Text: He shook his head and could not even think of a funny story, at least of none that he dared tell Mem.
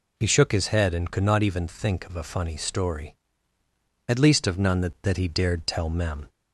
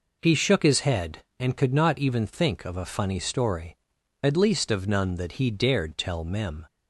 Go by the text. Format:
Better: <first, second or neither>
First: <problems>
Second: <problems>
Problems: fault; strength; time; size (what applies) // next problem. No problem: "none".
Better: second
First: says "that" twice; at 5.0 s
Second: none